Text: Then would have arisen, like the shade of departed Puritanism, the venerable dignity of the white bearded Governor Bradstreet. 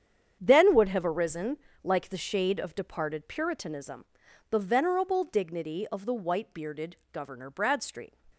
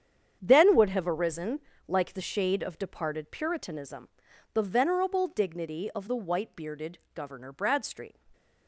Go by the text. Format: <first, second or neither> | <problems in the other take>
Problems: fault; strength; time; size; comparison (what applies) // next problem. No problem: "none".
neither | starts louder than the rest; strong; the same in both // pauses between "bearded" and "Governor"; slight; the same in both